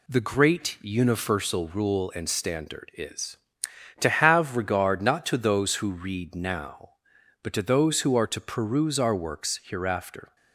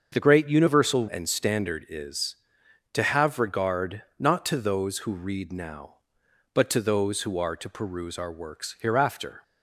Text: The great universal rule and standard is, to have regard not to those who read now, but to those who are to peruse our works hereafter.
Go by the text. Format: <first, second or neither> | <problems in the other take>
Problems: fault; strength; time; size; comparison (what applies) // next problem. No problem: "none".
first | starts louder than the rest; until 1.1 s; 6.5 dB // skips "rule"; at 1.0 s // pauses between "regard" and "not"; slight; at 4.0 s; 0.18 s long